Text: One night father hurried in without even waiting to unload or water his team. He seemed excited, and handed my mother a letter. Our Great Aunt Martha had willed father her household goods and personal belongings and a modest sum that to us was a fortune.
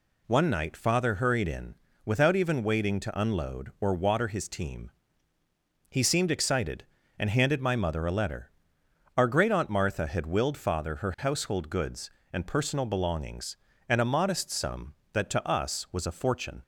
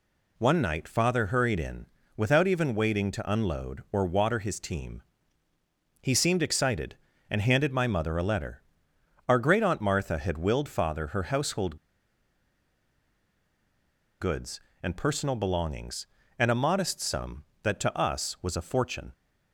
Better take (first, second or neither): first